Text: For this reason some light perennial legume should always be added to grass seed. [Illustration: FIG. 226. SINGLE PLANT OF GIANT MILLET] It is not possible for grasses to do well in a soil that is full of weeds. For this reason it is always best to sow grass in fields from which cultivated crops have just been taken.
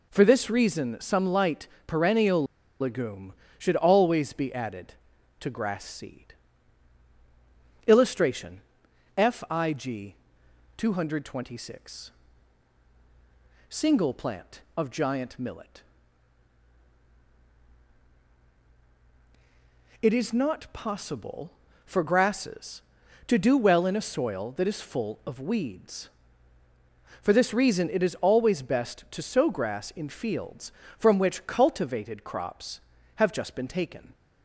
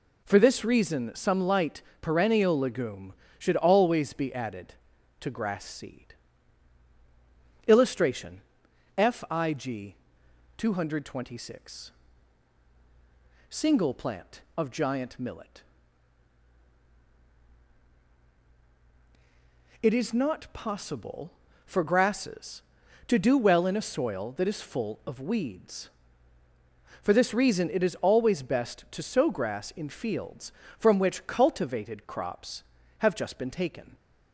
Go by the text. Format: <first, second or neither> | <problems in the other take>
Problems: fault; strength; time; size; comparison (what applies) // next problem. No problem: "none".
second | pauses between "light" and "perennial"; slight; at 1.6 s; 0.18 s long; slight in the second // pauses between "perennial" and "legume"; at 2.4 s; 0.36 s long // pauses between "MILLET" and "It"; strong; at 15.8 s; 4.1 s long; strong in the second